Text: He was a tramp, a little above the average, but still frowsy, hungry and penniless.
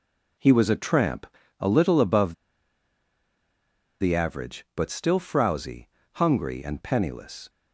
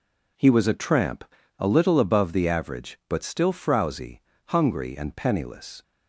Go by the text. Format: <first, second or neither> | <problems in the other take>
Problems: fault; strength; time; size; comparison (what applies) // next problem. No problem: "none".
second | pauses between "above" and "the"; strong; at 2.3 s; 1.6 s long